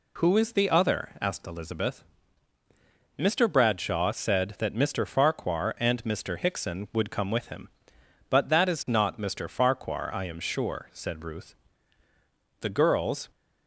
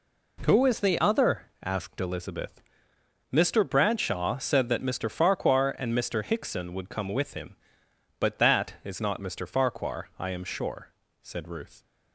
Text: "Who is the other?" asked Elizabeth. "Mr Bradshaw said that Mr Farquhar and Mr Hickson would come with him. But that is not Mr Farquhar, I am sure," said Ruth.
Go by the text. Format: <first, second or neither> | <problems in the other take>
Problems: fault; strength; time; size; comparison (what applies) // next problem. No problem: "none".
second | goes on to say "The girls"; noticeable; from 12.5 s on; 0.70 s long